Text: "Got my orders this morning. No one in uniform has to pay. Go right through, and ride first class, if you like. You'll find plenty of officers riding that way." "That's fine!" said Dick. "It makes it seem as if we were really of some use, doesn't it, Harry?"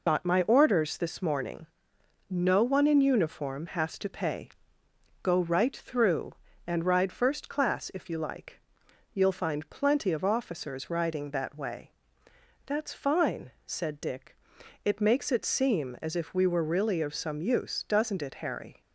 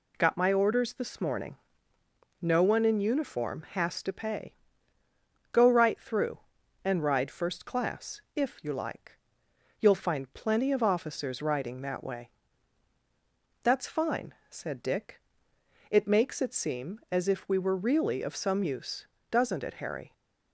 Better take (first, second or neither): second